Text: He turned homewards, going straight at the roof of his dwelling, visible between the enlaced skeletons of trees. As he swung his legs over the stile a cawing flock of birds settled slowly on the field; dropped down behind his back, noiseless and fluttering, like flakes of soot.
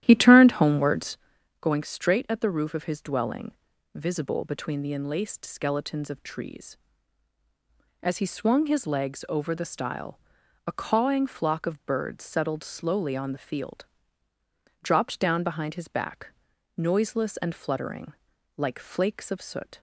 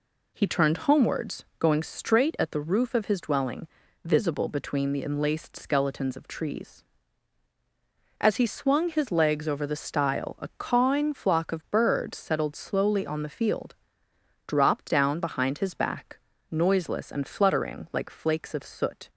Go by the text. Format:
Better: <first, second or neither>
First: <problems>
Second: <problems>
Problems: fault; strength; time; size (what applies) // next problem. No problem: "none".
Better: second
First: starts louder than the rest; strong; until 1.6 s; 12 dB // pauses between "stile" and "a"; noticeable; at 10.1 s; 0.48 s long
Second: none